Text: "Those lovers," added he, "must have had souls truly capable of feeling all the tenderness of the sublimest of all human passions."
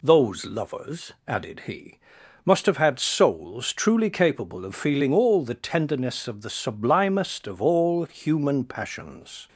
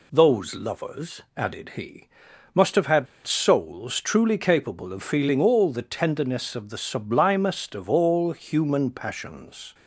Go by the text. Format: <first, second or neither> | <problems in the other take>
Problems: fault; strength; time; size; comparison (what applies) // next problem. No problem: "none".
first | pauses between "had" and "souls"; slight; at 3.0 s; 0.19 s long